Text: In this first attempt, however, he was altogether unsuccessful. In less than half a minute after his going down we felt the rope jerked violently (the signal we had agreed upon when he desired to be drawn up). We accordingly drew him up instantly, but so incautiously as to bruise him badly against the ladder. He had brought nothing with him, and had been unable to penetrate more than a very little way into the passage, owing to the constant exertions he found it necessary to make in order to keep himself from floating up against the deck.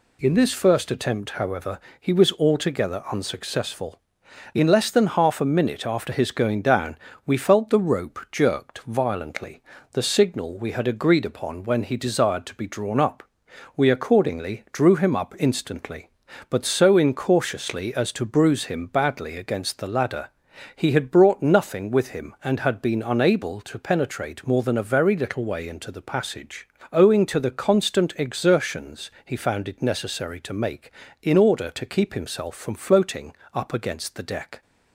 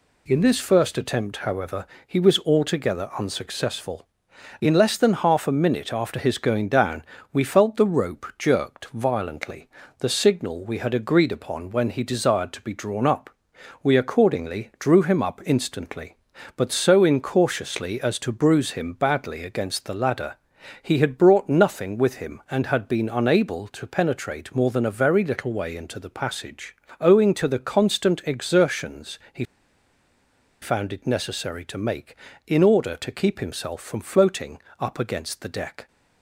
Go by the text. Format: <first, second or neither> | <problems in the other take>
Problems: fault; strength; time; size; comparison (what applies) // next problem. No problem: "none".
first | pauses between "down" and "we"; slight; at 7.0 s; 0.30 s long; slight in the first // pauses between "exertions" and "he"; slight; at 29.1 s; 0.16 s long; slight in the first // pauses between "he" and "found"; at 29.4 s; 1.1 s long // pauses between "floating" and "up"; slight; at 34.5 s; 0.20 s long; slight in the first